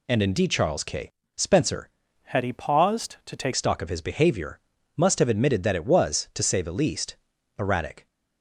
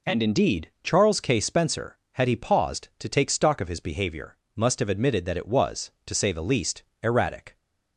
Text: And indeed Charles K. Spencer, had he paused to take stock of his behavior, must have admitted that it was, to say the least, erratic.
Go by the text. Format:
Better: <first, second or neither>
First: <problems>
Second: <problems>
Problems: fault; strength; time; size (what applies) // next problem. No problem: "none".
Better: second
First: changes voice from "had" to "take"; from 2.2 to 3.5 s; 1.3 s long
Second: none